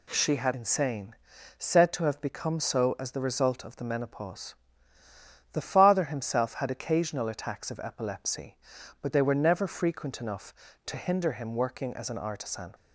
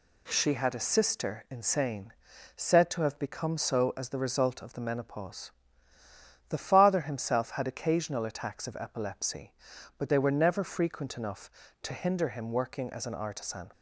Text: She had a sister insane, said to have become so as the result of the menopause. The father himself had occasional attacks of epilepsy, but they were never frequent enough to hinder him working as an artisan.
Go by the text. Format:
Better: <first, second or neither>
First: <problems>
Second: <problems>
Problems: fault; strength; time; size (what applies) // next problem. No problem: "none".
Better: second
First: skips "a sister"; at 0.5 s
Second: none